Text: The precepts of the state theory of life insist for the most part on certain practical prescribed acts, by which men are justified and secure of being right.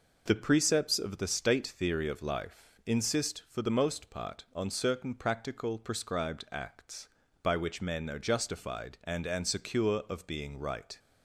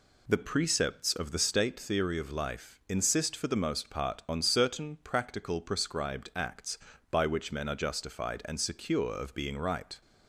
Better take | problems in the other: second | says "and" twice; at 9.2 s

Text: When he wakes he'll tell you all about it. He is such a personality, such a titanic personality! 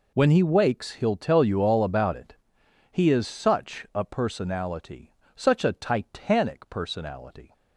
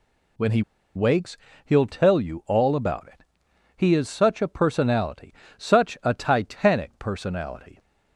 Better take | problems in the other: first | pauses between "he" and "wakes"; slight; at 0.6 s; 0.33 s long // pauses between "wakes" and "he'll"; slight; at 1.3 s; 0.28 s long

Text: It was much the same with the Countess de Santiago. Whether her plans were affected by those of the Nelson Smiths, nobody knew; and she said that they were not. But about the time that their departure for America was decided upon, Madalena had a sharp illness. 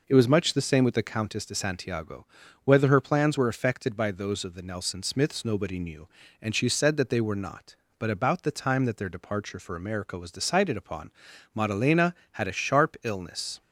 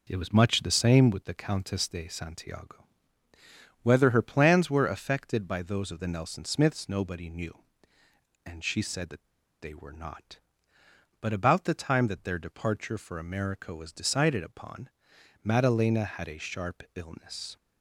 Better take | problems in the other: first | pauses between "that" and "they"; slight; at 9.2 s; 0.34 s long

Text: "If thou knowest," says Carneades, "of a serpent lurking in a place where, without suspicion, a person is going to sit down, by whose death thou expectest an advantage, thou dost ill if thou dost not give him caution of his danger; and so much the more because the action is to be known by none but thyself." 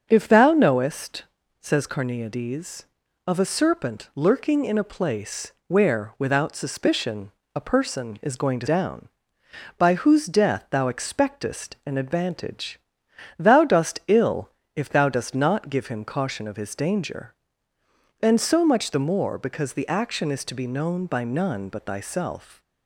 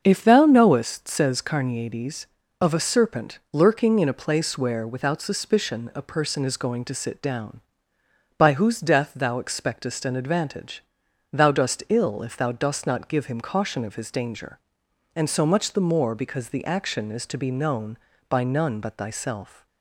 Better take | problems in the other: second | starts louder than the rest; until 1.1 s; 7 dB; also in the second // skips "sit"; at 8.6 s // pauses between "ill" and "if"; slight; at 14.4 s; 0.26 s long

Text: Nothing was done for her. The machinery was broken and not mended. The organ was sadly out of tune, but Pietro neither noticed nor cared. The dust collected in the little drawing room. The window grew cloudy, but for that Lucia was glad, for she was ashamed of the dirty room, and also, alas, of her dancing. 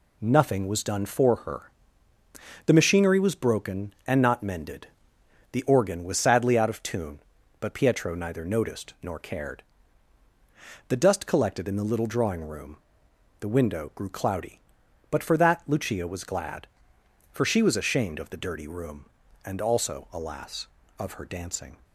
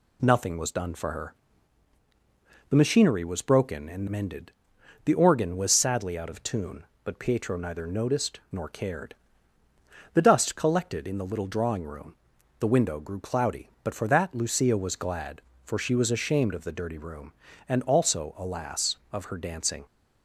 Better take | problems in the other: first | skips "not"; at 4.0 s

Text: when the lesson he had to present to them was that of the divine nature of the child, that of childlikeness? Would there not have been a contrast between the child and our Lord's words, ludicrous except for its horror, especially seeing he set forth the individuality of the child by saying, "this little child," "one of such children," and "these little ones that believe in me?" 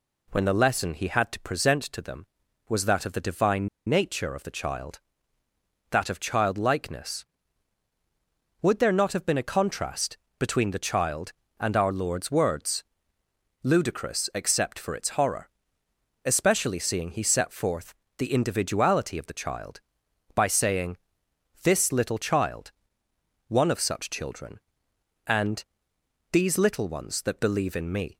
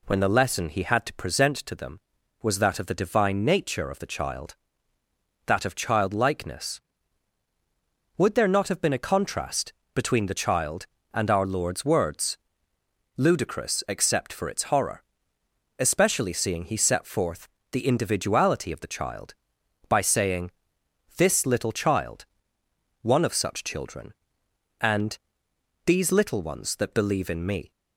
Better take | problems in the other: second | pauses between "divine" and "nature"; slight; at 3.6 s; 0.20 s long // pauses between "contrast" and "between"; slight; at 10.1 s; 0.22 s long; slight in the second // pauses between "forth" and "the"; slight; at 17.9 s; 0.24 s long; slight in the second // pauses between "and" and "these"; noticeable; at 25.6 s; 0.66 s long; noticeable in the second

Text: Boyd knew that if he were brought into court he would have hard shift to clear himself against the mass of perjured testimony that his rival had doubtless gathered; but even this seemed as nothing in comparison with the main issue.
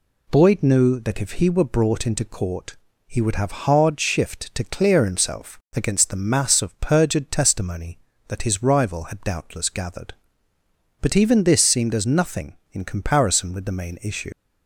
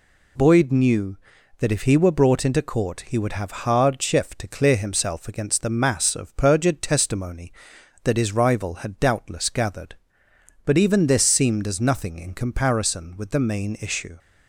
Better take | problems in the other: second | pauses between "court" and "he"; slight; at 2.7 s; 0.32 s long // pauses between "himself" and "against"; slight; at 5.5 s; 0.18 s long // leaves "issue" unfinished; at 14.3 s; 95 ms

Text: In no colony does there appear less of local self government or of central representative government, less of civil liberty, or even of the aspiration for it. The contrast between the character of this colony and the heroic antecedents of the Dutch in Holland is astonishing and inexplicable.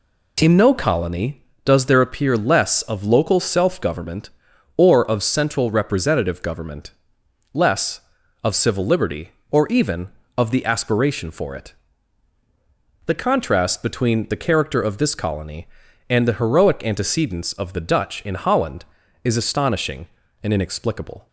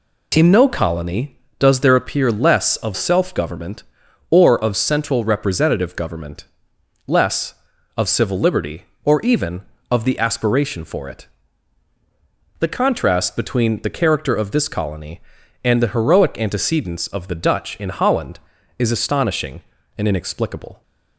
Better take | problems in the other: first | skips "local"; at 2.9 s

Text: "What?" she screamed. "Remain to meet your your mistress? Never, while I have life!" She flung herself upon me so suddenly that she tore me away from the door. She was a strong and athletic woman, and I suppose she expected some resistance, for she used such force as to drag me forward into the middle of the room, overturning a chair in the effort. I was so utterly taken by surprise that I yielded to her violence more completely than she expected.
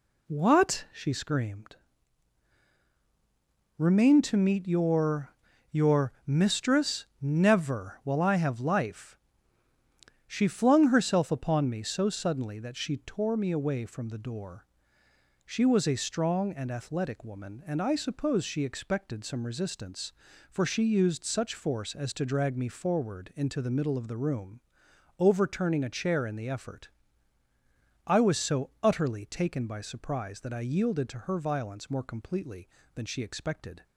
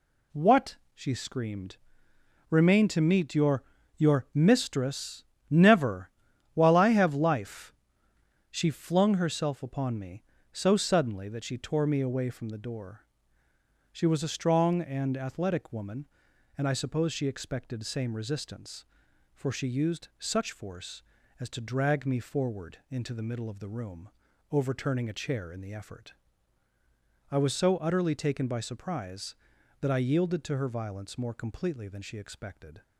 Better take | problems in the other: first | pauses between "your" and "your"; slight; at 3.6 s; 0.34 s long; also in the first // says "same" for "some"; at 17.8 s

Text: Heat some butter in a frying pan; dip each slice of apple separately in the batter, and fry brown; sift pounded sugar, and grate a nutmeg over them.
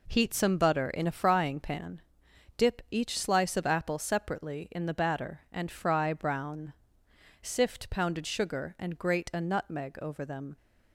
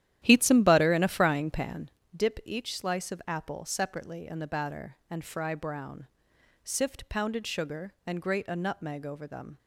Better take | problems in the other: first | starts louder than the rest; strong; until 2.1 s; 12 dB

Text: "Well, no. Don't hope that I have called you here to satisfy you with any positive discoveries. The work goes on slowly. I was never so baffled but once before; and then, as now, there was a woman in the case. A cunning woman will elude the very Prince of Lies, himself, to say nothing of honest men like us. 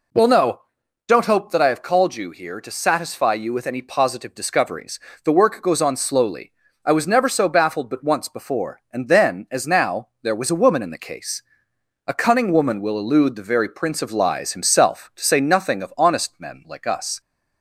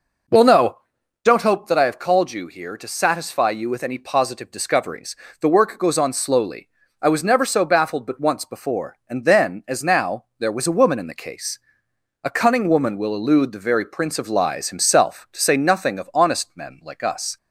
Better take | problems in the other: first | starts louder than the rest; noticeable; until 1.3 s; 5 dB

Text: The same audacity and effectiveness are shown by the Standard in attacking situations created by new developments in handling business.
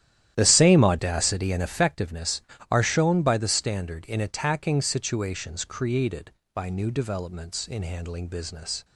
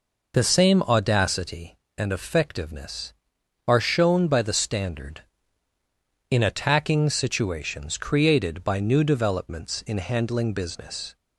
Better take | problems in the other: second | starts louder than the rest; strong; until 1.9 s; 11.5 dB

